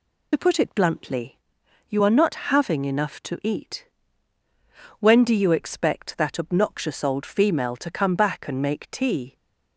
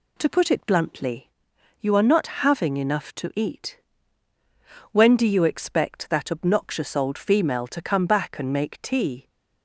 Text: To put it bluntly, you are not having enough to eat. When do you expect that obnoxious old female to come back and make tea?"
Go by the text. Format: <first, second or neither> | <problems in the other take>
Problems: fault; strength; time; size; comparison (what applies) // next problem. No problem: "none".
second | loses the start of "To"; at 0.3 s; 60 ms